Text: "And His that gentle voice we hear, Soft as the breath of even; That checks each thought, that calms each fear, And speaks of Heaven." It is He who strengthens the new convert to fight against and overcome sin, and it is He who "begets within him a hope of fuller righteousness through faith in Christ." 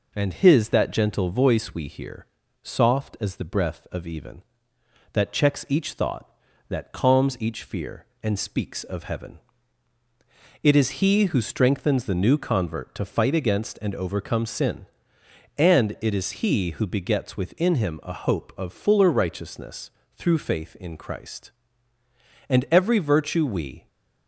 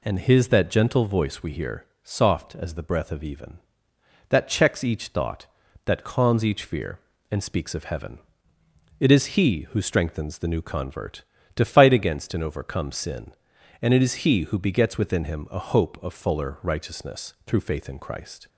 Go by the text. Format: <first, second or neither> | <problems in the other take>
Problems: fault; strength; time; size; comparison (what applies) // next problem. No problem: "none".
second | pauses between "righteousness" and "through"; slight; at 19.9 s; 0.24 s long // goes on to say "And every virtue we"; from 22.4 s on; 1.3 s long